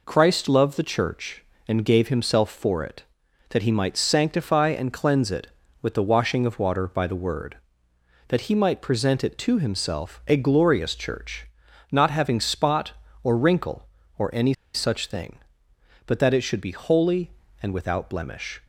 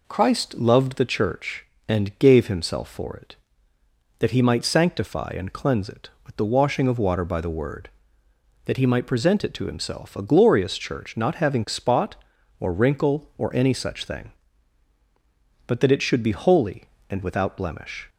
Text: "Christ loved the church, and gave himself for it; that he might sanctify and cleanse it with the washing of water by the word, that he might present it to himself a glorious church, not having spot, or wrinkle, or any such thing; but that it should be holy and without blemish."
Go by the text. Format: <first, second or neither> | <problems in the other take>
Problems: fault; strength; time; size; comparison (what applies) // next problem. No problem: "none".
second | pauses between "any" and "such"; slight; at 14.5 s; 0.21 s long